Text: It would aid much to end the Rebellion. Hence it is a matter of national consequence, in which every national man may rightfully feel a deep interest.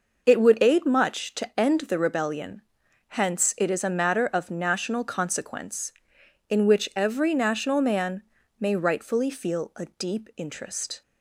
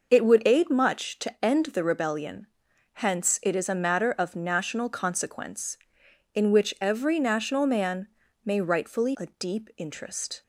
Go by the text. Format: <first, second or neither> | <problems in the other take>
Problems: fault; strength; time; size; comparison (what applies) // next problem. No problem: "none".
first | pauses between "man" and "may"; at 8.0 s; 0.38 s long; also in the first // skips "feel"; at 9.1 s